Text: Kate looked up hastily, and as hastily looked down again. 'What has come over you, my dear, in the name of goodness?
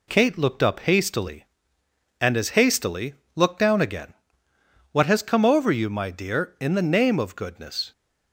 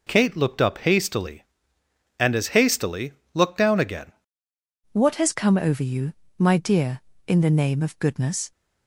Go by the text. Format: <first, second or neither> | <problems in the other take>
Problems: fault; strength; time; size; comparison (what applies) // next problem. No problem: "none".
first | pauses between "hastily" and "looked"; slight; at 3.1 s; 0.22 s long; slight in the first // changes voice at "What"; from 4.9 s on; 3.6 s long